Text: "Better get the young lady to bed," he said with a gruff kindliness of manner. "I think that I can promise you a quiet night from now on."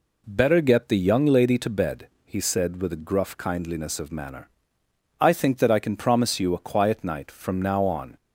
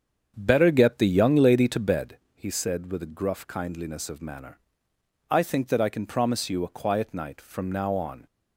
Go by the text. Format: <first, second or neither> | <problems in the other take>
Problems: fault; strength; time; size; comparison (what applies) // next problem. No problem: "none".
first | starts louder than the rest; strong; until 2.2 s; 7.5 dB